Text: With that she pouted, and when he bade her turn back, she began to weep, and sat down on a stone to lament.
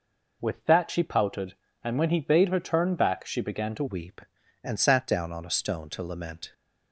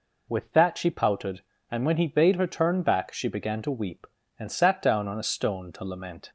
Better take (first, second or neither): second